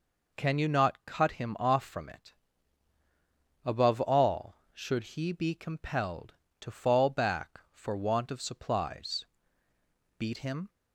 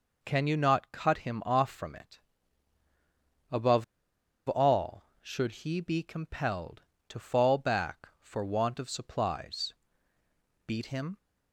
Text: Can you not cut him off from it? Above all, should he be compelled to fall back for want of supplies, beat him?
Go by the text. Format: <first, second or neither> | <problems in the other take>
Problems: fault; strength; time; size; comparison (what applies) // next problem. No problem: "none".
first | pauses between "Above" and "all"; noticeable; at 3.8 s; 0.64 s long